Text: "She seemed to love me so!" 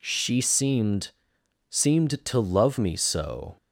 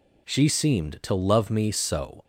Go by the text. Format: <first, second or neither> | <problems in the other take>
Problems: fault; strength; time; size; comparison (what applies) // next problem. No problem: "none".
second | says "seemed" twice; at 1.6 s